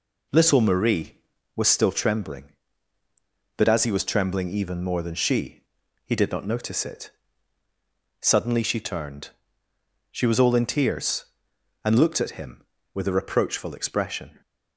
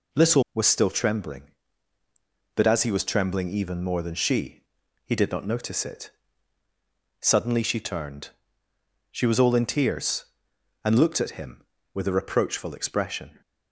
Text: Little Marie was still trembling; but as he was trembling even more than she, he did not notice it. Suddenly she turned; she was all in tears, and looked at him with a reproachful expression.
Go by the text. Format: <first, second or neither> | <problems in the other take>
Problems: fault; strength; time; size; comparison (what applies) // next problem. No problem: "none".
first | skips "Marie"; at 0.4 s